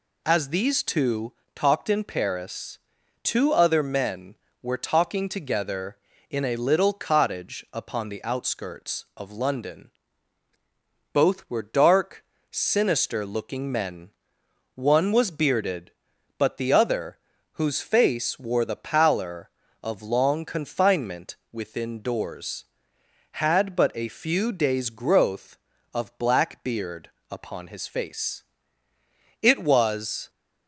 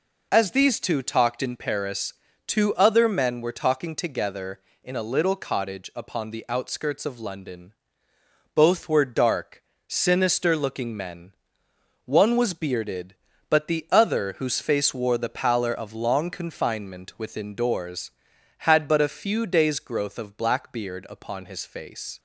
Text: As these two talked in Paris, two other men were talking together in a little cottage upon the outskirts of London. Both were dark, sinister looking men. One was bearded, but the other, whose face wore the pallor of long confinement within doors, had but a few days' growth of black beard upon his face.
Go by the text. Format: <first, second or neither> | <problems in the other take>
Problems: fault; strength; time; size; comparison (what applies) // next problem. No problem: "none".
second | pauses between "two" and "talked"; slight; at 1.3 s; 0.24 s long // pauses between "confinement" and "within"; slight; at 21.3 s; 0.16 s long // pauses between "beard" and "upon"; slight; at 27.0 s; 0.20 s long // goes on to say "It was"; noticeable; from 29.4 s on; 0.88 s long